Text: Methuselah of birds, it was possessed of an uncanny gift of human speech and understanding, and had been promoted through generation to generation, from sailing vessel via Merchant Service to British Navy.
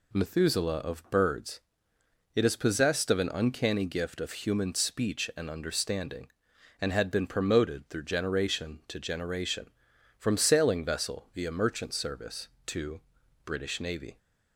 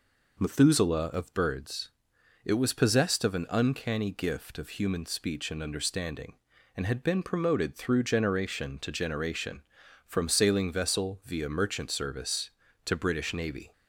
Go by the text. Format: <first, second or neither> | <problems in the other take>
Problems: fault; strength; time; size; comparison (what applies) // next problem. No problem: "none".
second | says "is" for "was"; at 2.4 s // pauses between "to" and "British"; noticeable; at 12.9 s; 0.46 s long